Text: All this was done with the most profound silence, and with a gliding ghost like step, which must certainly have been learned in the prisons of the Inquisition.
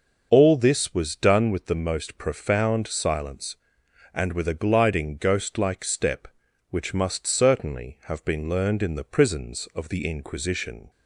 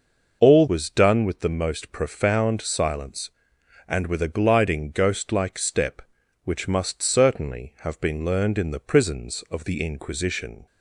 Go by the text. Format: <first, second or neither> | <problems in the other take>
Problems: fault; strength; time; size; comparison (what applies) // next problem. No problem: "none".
first | skips "this"; at 0.6 s